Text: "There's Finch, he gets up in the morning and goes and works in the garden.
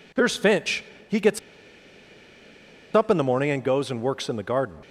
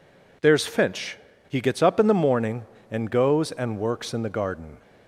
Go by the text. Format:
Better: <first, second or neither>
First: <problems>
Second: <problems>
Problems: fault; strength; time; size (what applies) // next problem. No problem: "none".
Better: second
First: pauses between "gets" and "up"; strong; at 1.3 s; 1.5 s long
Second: none